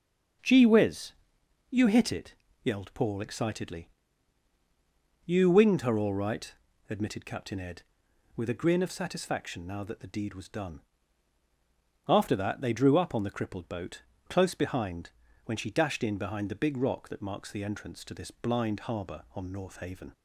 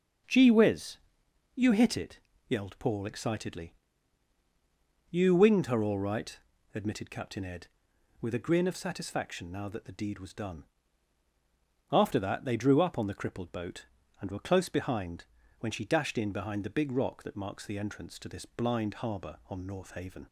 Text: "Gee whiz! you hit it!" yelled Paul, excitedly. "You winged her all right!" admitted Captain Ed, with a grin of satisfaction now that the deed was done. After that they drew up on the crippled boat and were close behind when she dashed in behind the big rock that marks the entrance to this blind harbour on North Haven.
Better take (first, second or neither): second